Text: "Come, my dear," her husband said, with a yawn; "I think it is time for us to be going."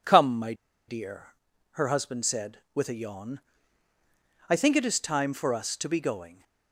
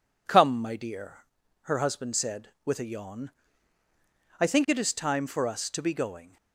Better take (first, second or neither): second